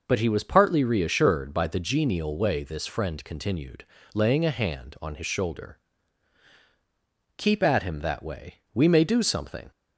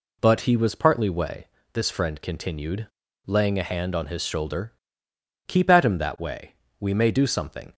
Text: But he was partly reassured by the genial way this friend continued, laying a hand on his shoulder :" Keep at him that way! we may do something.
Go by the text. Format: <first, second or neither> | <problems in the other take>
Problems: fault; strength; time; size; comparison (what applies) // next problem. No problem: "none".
first | skips "reassured by the genial"; at 1.0 s // pauses between "way" and "this"; slight; at 1.4 s; 0.26 s long